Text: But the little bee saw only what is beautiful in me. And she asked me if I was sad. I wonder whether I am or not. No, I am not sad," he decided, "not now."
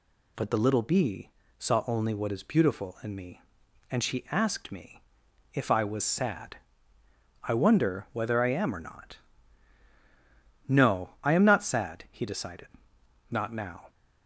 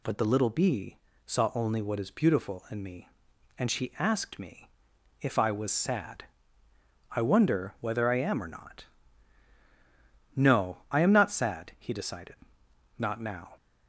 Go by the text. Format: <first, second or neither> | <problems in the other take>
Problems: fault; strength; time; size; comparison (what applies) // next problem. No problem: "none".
neither | pauses between "bee" and "saw"; slight; the same in both // pauses between "me" and "if"; noticeable; the same in both